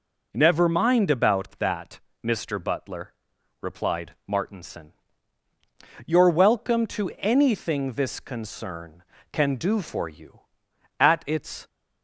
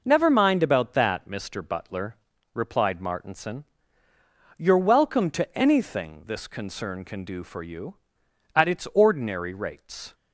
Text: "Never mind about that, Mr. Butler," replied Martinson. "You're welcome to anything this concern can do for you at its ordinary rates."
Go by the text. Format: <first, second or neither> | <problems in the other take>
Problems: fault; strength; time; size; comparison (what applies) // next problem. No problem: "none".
second | stops before "ordinary rates"; at 11.6 s